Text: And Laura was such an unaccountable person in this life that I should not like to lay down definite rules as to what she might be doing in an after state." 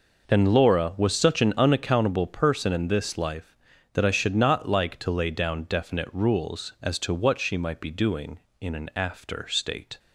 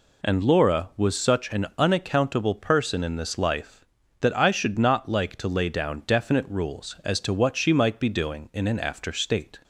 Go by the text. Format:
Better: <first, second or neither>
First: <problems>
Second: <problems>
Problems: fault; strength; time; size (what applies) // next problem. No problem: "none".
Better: neither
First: none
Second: none